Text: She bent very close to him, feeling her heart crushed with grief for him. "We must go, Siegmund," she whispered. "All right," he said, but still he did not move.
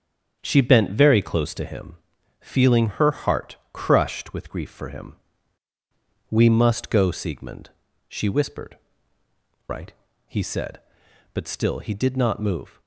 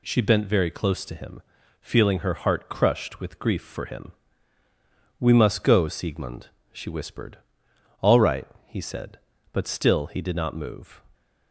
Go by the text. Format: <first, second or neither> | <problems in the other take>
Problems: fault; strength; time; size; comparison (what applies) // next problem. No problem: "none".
second | starts louder than the rest; strong; until 1.4 s; 7.5 dB // pauses between "heart" and "crushed"; slight; at 3.5 s; 0.16 s long // skips "All"; at 9.2 s